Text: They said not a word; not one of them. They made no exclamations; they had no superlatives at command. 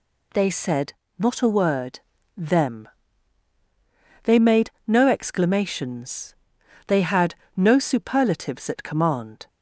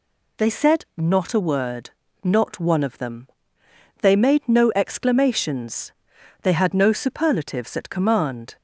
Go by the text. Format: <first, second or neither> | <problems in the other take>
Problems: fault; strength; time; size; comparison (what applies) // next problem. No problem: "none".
second | pauses between "said" and "not"; slight; at 0.9 s; 0.24 s long // skips "not one of"; at 2.1 s // pauses between "made" and "no"; slight; at 4.6 s; 0.18 s long // pauses between "had" and "no"; slight; at 7.3 s; 0.24 s long